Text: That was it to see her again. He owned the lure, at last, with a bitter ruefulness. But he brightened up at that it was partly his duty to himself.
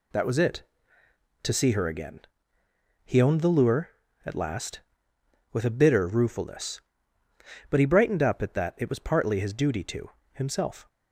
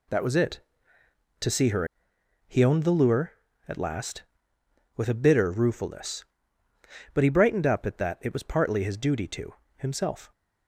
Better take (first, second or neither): first